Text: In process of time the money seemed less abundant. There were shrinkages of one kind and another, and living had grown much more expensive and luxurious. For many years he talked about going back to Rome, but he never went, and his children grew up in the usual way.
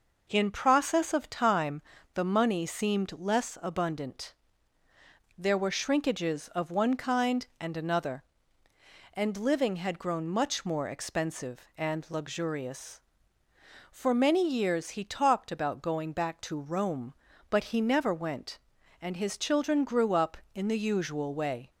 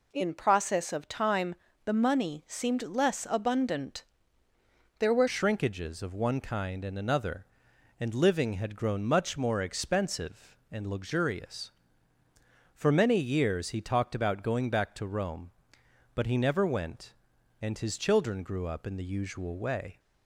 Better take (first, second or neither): first